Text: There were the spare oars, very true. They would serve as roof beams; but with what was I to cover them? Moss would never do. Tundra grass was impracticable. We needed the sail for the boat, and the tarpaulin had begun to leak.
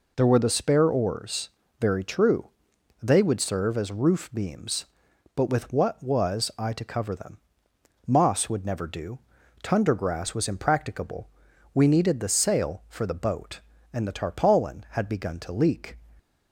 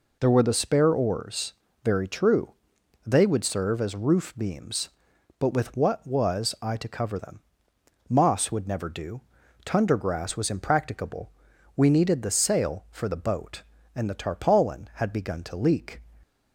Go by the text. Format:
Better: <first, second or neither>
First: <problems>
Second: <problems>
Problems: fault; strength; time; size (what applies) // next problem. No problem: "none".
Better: neither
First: none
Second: none